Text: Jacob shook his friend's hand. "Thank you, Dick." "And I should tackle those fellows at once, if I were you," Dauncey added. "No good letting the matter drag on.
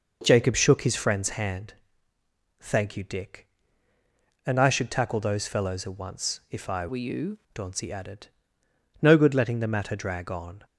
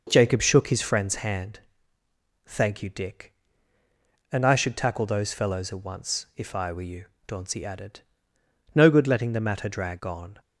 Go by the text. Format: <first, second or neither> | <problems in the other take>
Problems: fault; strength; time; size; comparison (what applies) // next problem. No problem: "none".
second | changes voice from "were" to "you"; from 6.8 to 7.3 s; 0.5 s long